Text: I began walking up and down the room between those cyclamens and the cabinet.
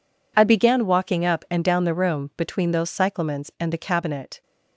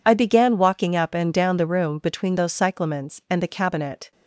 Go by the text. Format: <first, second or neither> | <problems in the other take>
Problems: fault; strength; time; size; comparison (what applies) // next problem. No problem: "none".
neither | none